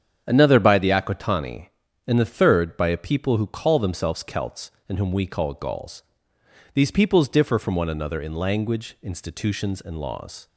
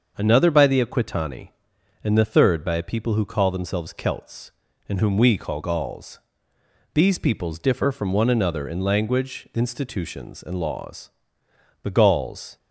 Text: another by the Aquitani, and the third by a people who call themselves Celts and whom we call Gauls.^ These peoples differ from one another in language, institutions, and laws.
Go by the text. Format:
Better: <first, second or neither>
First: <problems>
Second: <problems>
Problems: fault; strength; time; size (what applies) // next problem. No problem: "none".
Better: first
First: starts louder than the rest; strong; until 1.2 s; 8 dB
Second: starts louder than the rest; until 1.1 s; 6.5 dB // goes on to say "The Gauls"; noticeable; from 11.8 s on; 0.74 s long